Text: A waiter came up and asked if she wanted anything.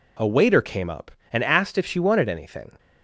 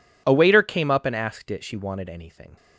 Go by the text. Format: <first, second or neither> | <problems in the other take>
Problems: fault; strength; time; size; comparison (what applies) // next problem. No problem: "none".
first | says "it" for "if"; at 1.4 s